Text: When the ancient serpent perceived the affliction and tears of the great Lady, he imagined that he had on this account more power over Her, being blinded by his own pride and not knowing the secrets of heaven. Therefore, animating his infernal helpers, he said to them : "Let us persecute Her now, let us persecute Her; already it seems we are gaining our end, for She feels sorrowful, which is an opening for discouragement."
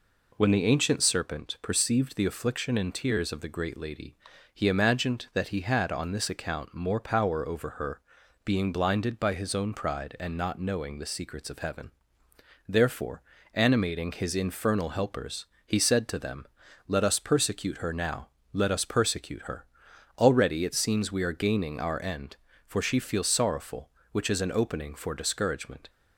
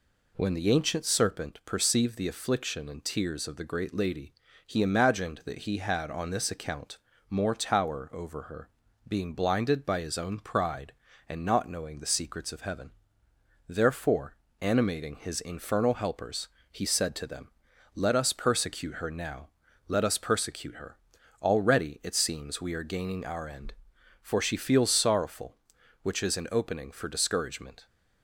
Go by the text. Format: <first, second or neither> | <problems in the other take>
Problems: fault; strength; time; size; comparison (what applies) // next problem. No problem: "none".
first | pauses between "account" and "more"; slight; at 6.9 s; 0.32 s long // says "tower" for "power"; at 7.5 s